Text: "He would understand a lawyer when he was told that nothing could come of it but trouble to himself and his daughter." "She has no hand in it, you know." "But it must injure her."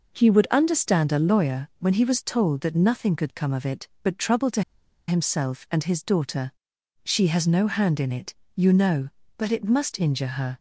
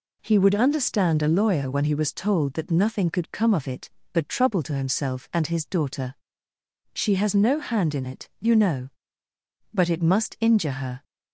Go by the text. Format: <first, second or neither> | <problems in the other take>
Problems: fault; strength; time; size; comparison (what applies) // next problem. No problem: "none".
second | pauses between "to" and "himself"; noticeable; at 4.6 s; 0.47 s long